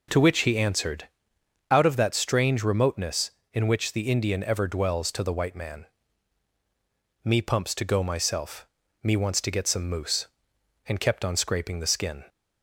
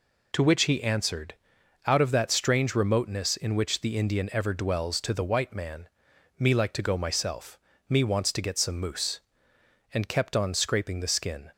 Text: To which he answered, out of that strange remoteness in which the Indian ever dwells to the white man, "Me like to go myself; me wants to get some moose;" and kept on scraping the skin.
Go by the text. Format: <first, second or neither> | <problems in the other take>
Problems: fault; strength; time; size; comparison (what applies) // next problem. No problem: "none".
second | says "pumps" for "like"; at 7.4 s